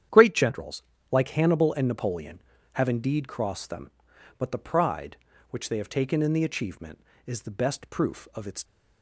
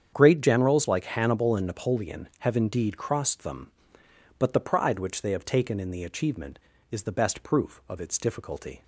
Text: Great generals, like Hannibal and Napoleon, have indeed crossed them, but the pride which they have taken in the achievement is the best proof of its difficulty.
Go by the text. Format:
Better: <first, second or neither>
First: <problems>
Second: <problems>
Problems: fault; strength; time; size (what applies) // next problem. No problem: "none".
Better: second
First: starts louder than the rest; strong; until 1.4 s; 9.5 dB // stops before "difficulty"; at 8.6 s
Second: starts louder than the rest; strong; until 1.1 s; 8 dB